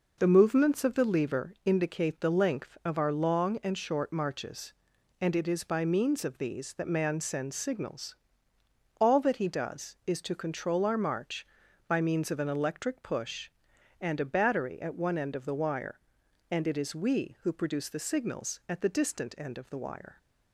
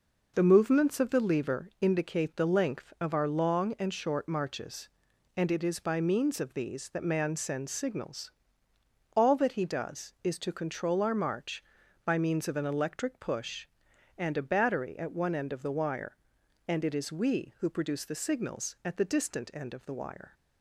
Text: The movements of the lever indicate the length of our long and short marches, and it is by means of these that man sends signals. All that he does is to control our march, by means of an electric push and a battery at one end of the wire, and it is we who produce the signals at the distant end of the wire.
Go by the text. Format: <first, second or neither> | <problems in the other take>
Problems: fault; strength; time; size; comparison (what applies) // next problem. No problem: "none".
neither | none